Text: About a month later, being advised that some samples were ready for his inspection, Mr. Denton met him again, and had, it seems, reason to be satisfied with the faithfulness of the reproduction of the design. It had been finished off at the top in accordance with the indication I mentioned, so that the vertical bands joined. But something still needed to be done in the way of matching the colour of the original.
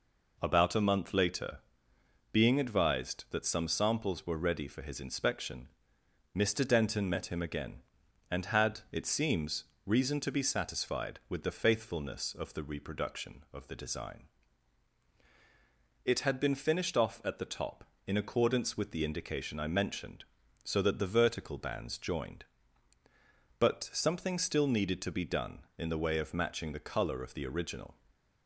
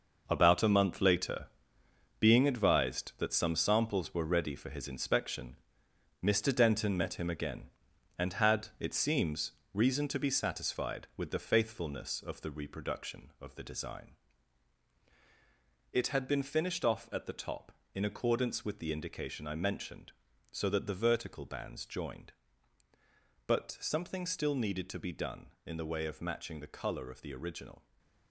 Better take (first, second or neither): first